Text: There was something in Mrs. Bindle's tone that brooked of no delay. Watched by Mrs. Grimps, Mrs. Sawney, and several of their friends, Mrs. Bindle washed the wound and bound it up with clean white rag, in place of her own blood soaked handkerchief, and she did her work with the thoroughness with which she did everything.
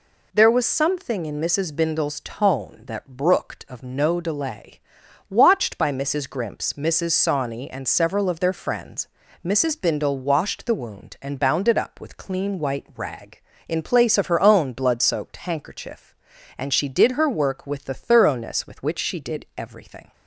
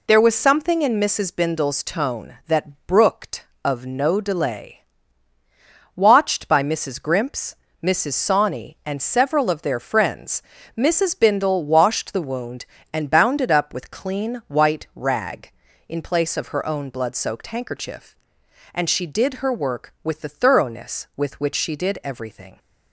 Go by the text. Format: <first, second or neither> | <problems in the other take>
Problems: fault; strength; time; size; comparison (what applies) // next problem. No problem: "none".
neither | none